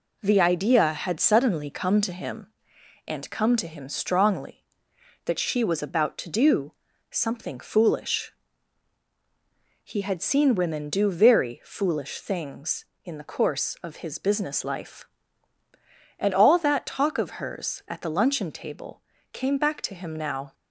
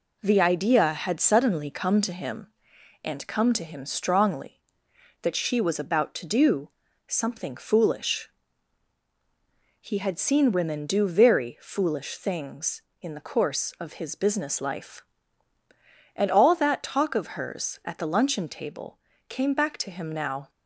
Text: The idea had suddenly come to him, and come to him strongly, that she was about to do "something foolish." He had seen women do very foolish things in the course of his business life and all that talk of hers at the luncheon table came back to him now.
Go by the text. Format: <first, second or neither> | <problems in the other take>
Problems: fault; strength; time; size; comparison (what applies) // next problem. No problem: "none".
neither | pauses between "do" and "something"; slight; the same in both // pauses between "table" and "came"; slight; the same in both